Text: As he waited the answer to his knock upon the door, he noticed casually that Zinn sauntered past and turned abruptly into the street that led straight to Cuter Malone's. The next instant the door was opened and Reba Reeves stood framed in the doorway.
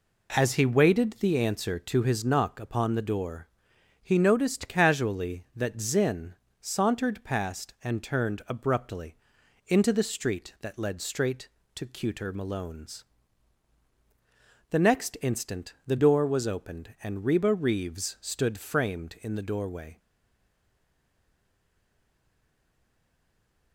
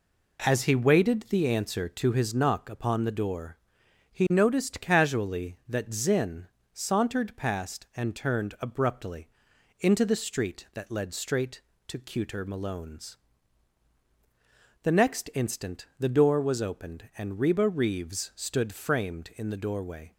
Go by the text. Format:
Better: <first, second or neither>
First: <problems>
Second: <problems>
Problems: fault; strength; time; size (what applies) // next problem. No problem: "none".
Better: second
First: pauses between "Zinn" and "sauntered"; slight; at 6.3 s; 0.26 s long // pauses between "abruptly" and "into"; noticeable; at 9.1 s; 0.52 s long // stays silent after the last word; strong; from 19.9 s on; 3.8 s long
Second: pauses between "Zinn" and "sauntered"; slight; at 6.4 s; 0.26 s long // pauses between "abruptly" and "into"; noticeable; at 9.2 s; 0.52 s long